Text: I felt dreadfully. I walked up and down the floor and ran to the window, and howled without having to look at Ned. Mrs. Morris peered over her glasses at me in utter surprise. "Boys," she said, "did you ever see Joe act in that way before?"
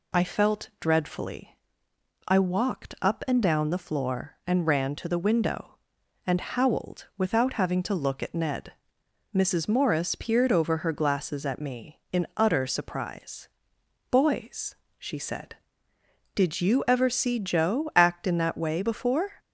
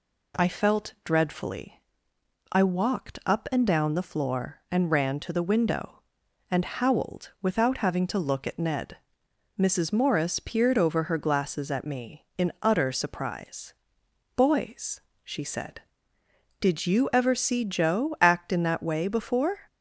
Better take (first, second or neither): second